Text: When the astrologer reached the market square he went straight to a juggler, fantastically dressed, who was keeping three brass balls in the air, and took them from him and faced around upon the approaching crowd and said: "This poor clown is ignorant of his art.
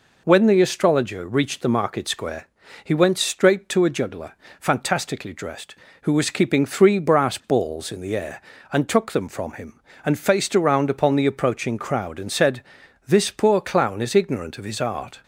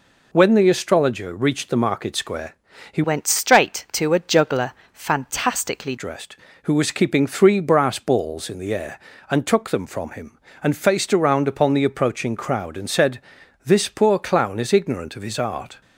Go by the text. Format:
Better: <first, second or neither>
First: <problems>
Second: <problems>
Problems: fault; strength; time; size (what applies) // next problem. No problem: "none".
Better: first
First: pauses between "square" and "he"; at 2.4 s; 0.38 s long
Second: pauses between "square" and "he"; at 2.5 s; 0.38 s long // changes voice from "went" to "fantastically"; from 3.0 to 5.9 s; 2.9 s long